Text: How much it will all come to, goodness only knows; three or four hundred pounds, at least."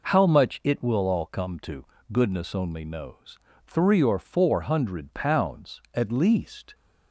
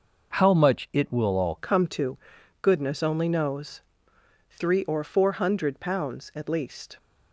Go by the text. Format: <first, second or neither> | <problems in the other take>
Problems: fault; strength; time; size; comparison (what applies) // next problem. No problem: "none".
first | changes voice at "come"; from 1.5 s on; 5.4 s long